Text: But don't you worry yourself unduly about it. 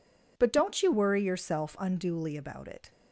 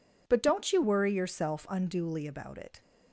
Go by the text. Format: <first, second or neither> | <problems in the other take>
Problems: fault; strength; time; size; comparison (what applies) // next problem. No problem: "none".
neither | none